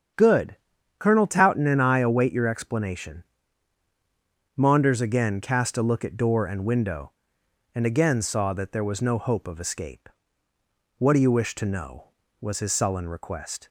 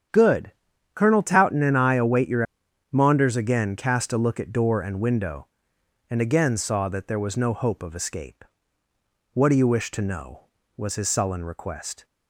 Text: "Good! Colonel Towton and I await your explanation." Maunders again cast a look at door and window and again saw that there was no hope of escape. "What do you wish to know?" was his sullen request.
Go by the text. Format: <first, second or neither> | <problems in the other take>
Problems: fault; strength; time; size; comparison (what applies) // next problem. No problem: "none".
first | starts louder than the rest; strong; until 1.5 s; 8.5 dB; strong in the first // skips "explanation"; at 2.6 s